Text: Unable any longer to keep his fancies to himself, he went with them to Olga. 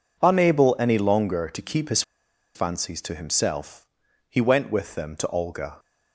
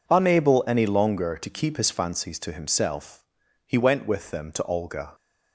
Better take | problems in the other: second | pauses between "his" and "fancies"; noticeable; at 2.0 s; 0.53 s long

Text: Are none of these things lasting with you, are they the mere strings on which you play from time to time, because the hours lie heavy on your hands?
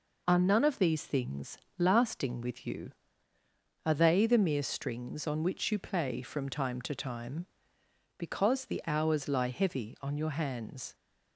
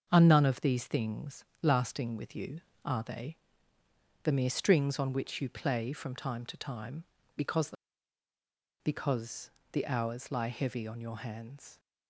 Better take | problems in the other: first | starts louder than the rest; until 1.1 s; 6.5 dB // pauses between "things" and "lasting"; slight; at 1.4 s; 0.18 s long; slight in the first // pauses between "they" and "the"; noticeable; at 3.3 s; 0.88 s long // says "because" twice; at 8.8 s

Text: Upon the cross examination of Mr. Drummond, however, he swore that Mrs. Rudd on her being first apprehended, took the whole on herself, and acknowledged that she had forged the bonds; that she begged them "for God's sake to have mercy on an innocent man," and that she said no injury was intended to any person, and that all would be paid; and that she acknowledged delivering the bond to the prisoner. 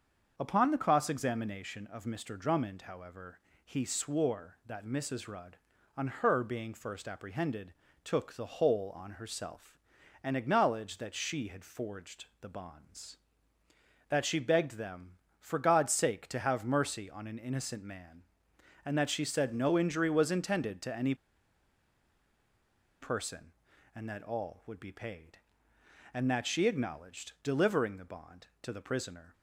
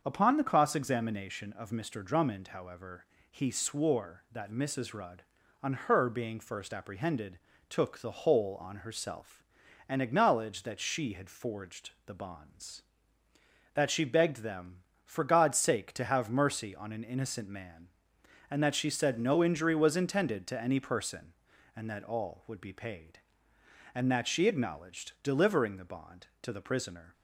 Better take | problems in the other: second | starts louder than the rest; until 1.3 s; 6.5 dB; also in the second // pauses between "forged" and "the"; slight; at 12.2 s; 0.16 s long; slight in the second // pauses between "any" and "person"; strong; at 21.1 s; 1.8 s long

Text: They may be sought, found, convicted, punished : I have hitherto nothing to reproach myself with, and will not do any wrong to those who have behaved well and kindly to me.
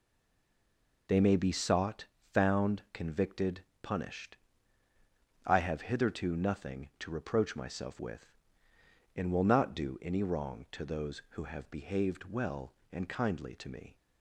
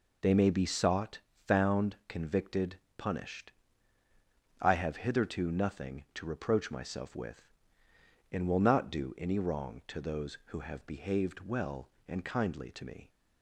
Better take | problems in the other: second | stays silent before the first word; until 1.0 s; 1.0 s long

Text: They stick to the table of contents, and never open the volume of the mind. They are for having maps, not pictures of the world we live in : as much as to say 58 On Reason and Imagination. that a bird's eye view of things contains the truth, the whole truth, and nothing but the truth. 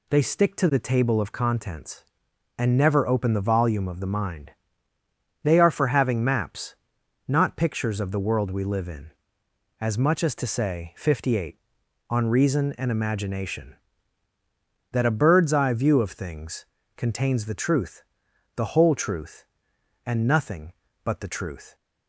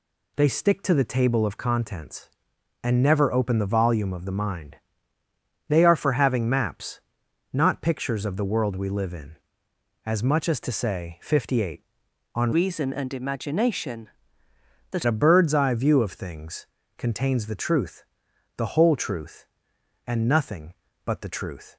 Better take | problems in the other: first | changes voice from "Reason" to "that"; from 12.5 to 15.0 s; 2.5 s long // pauses between "things" and "contains"; slight; at 16.6 s; 0.32 s long; slight in the first

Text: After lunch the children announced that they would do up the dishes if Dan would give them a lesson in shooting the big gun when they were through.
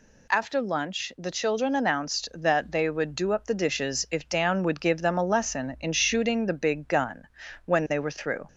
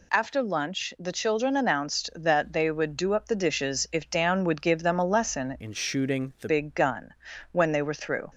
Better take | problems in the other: first | changes voice from "in" to "the"; from 5.5 to 6.4 s; 0.9 s long // pauses between "gun" and "when"; at 7.1 s; 0.40 s long; also in the first

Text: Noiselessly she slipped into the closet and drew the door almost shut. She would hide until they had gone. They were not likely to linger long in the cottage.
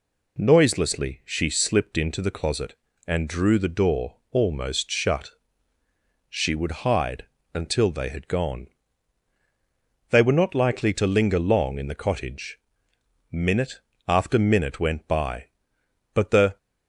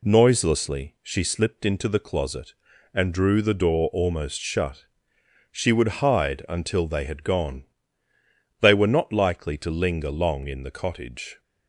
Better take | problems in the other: second | pauses between "door" and "almost"; slight; at 4.1 s; 0.16 s long // pauses between "hide" and "until"; slight; at 7.2 s; 0.30 s long // goes on to say "Minute after minute went by but the"; strong; from 13.3 s on; 3.2 s long

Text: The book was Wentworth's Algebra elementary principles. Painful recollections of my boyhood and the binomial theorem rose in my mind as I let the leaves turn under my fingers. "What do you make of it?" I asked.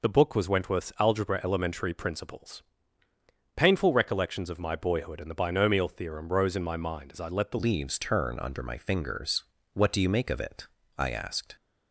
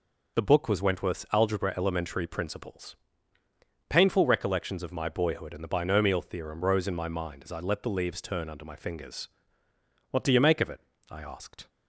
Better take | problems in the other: second | changes voice at "leaves"; from 7.5 s on; 4.0 s long

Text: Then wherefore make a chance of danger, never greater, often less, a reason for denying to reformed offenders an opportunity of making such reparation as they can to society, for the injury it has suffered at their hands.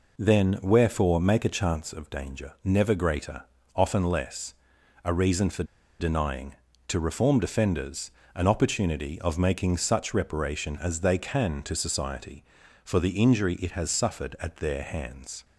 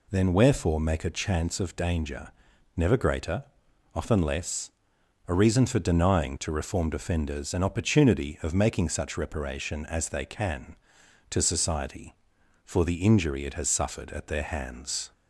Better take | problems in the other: second | pauses between "for" and "denying"; slight; at 5.6 s; 0.36 s long // pauses between "offenders" and "an"; slight; at 8.1 s; 0.24 s long

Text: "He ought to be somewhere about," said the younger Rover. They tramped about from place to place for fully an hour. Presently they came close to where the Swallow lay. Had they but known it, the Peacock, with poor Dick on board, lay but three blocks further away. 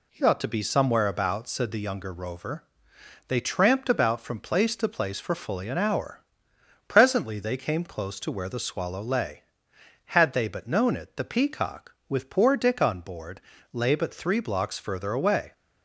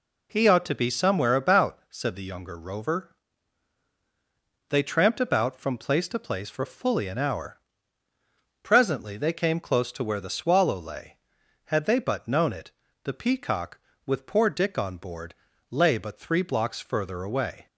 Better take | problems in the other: neither | none

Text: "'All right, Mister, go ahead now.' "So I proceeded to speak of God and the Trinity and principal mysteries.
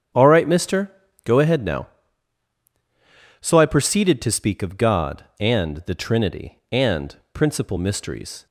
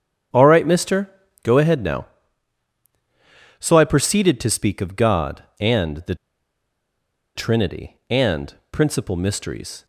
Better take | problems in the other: first | starts louder than the rest; strong; until 1.6 s; 9 dB; strong in the first // pauses between "the" and "Trinity"; at 6.1 s; 1.2 s long // pauses between "and" and "principal"; slight; at 8.5 s; 0.18 s long; slight in the first

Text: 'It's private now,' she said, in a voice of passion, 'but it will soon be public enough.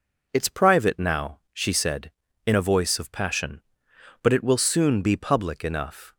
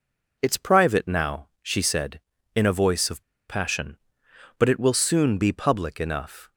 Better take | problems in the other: first | pauses between "of" and "passion"; slight; at 3.2 s; 0.25 s long

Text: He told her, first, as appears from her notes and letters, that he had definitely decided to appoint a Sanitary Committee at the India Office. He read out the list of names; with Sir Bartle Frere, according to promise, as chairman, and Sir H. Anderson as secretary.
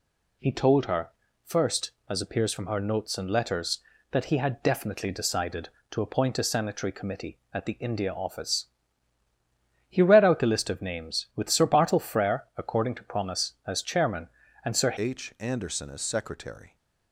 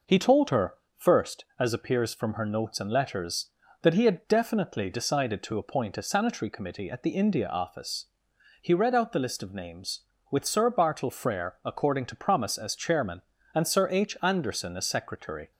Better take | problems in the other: second | changes voice at "H"; from 14.9 s on; 1.8 s long

